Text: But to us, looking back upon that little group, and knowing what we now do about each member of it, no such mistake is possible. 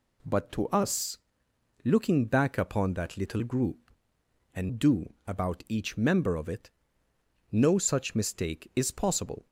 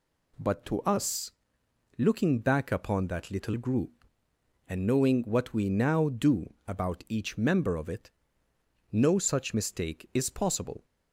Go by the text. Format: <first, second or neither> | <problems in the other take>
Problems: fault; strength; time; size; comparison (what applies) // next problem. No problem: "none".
second | skips "knowing what we now"; at 4.6 s